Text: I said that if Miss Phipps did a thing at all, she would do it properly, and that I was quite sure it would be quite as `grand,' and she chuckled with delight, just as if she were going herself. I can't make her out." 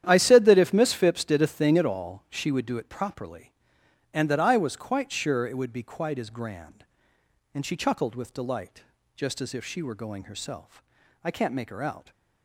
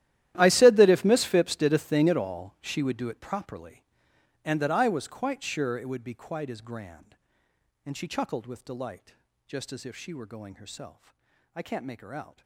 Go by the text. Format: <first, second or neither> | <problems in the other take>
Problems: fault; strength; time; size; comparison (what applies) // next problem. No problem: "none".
first | gets quieter; strong; throughout; 18.5 dB // starts louder than the rest; strong; until 1.3 s; 13 dB; strong in the first